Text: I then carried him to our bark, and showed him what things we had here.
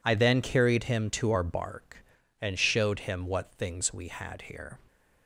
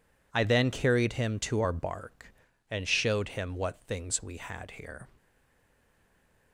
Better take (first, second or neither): first